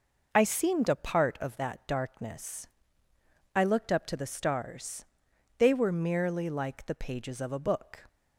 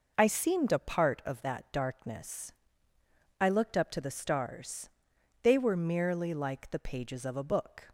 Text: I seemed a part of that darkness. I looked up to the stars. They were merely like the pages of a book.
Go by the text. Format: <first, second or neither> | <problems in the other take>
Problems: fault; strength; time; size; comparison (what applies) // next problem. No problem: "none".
neither | none